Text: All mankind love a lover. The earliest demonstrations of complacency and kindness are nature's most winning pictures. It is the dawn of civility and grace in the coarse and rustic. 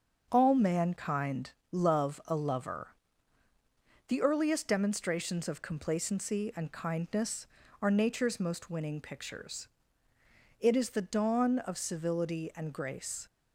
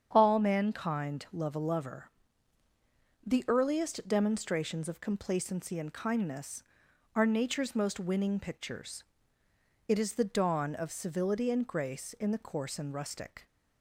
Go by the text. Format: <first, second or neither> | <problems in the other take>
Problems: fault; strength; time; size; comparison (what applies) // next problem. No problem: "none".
second | starts louder than the rest; until 1.3 s; 7 dB; strong in the second // pauses between "mankind" and "love"; slight; at 1.5 s; 0.20 s long // stops before "in the coarse and rustic"; at 13.2 s